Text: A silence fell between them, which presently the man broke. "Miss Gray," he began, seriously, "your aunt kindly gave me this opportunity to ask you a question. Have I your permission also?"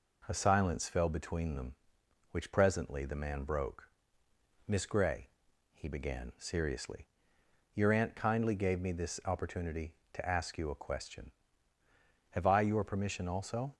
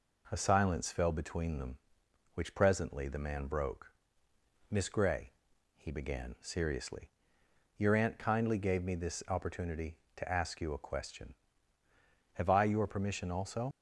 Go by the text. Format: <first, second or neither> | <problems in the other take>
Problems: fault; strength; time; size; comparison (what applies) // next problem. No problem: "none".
first | leaves "also" unfinished; at 13.7 s; 70 ms